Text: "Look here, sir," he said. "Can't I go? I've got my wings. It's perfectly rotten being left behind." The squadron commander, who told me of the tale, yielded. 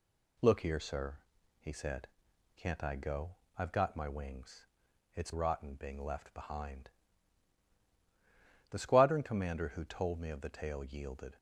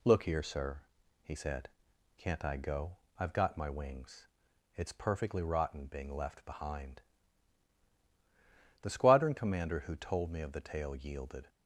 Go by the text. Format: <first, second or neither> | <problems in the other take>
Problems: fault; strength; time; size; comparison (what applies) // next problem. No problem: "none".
second | skips "perfectly"; at 5.3 s